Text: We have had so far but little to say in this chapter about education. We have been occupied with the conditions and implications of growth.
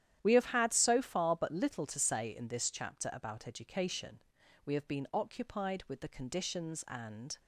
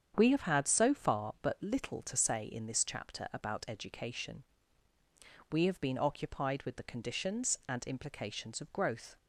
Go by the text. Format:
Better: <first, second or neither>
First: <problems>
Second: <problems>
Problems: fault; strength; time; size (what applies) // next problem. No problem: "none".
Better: second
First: starts louder than the rest; strong; until 1.2 s; 11 dB // stops before "implications of growth"; at 7.3 s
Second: starts louder than the rest; strong; until 1.1 s; 8 dB